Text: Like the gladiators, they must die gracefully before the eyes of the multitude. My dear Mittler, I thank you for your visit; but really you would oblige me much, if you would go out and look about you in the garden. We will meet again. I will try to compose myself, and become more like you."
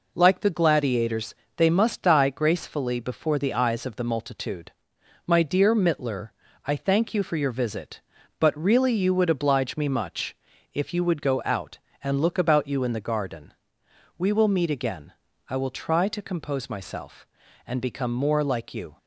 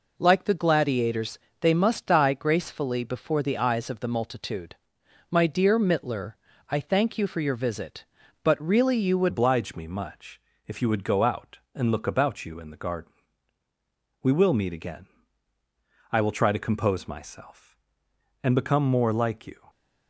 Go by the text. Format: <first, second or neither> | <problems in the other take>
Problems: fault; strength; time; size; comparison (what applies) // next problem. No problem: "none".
first | changes voice at "oblige"; from 9.2 s on; 10.4 s long